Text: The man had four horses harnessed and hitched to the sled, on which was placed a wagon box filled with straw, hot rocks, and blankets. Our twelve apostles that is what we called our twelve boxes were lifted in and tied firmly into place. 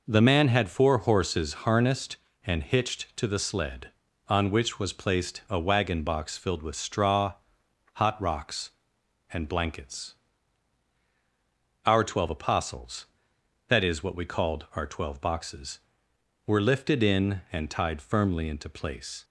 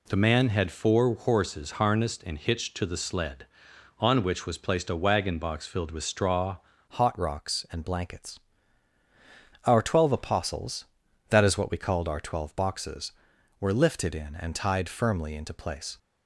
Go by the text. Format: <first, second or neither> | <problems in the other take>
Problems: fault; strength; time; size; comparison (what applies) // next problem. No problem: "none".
first | changes voice at "hot"; from 6.8 s on; 9.1 s long